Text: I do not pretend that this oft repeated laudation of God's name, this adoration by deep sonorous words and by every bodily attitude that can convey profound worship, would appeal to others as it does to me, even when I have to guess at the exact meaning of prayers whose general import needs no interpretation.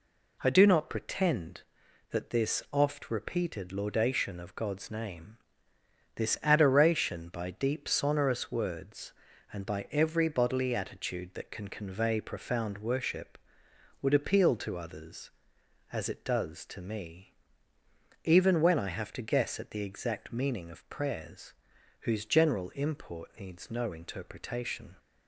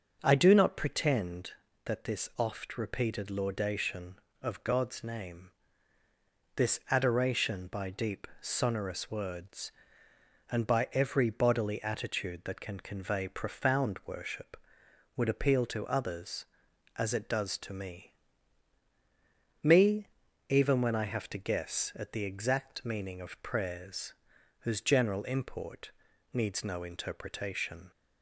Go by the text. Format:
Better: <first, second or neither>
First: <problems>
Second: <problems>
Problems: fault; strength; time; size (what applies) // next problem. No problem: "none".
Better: first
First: pauses between "prayers" and "whose"; noticeable; at 21.5 s; 0.48 s long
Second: starts louder than the rest; until 1.2 s; 6.5 dB // says "me" twice; at 19.6 s // pauses between "prayers" and "whose"; noticeable; at 24.1 s; 0.46 s long // pauses between "import" and "needs"; at 25.9 s; 0.42 s long